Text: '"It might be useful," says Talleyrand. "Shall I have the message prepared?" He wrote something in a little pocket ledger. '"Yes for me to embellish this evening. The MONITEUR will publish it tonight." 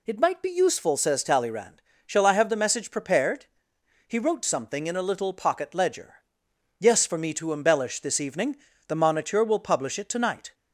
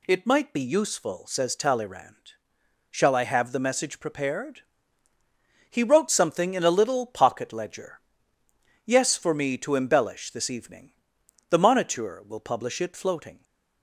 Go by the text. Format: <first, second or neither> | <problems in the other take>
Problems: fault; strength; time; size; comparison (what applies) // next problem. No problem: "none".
first | says "floating" for "tonight"; at 12.9 s